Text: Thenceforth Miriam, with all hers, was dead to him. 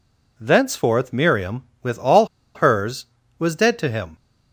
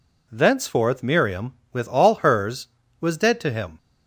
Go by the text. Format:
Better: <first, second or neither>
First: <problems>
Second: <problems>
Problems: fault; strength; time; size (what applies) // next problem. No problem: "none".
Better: second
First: pauses between "all" and "hers"; slight; at 2.2 s; 0.28 s long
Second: none